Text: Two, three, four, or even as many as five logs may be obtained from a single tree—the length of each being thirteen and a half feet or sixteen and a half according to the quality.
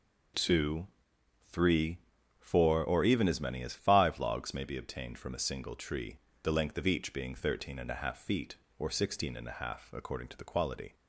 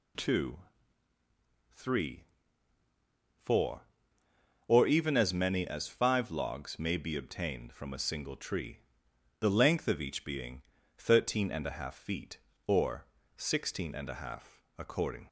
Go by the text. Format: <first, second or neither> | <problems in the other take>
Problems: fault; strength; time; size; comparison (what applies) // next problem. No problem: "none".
first | pauses between "being" and "thirteen"; slight; at 10.6 s; 0.36 s long // pauses between "or" and "sixteen"; slight; at 13.0 s; 0.32 s long // pauses between "half" and "according"; slight; at 14.6 s; 0.16 s long // stops before "to the quality"; at 15.2 s